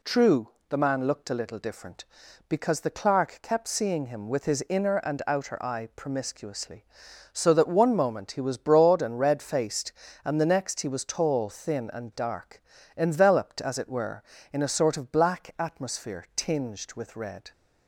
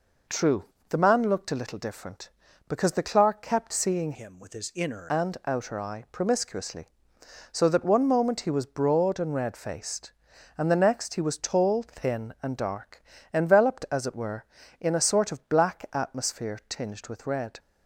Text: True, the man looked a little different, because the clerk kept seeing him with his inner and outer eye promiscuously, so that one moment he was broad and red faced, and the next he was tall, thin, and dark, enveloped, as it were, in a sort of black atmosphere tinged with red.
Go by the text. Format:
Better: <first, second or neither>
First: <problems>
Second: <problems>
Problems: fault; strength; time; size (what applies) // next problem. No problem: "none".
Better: first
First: none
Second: changes voice from "him" to "inner"; from 4.1 to 5.0 s; 0.9 s long